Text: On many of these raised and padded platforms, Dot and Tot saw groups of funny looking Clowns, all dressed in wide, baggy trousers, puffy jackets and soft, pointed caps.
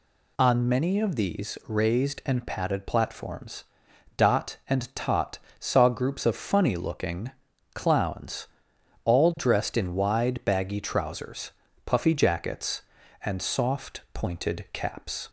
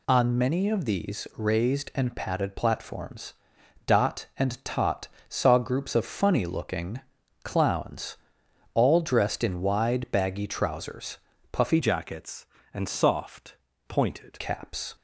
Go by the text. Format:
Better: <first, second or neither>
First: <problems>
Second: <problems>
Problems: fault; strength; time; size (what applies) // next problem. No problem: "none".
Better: first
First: pauses between "Tot" and "saw"; slight; at 5.3 s; 0.22 s long // pauses between "looking" and "Clowns"; at 7.3 s; 0.42 s long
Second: pauses between "Tot" and "saw"; slight; at 5.0 s; 0.22 s long // pauses between "looking" and "Clowns"; at 7.0 s; 0.42 s long // changes voice from "jackets" to "pointed"; from 11.8 to 14.4 s; 2.6 s long